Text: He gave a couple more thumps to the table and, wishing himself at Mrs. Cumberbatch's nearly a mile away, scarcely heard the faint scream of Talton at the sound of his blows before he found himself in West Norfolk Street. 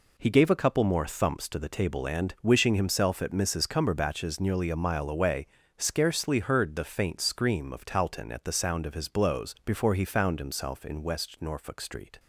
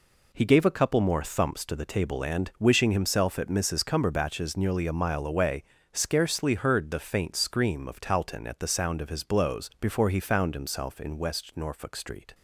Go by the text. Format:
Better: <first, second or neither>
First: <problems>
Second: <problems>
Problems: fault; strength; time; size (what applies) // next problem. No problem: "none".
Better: neither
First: none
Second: none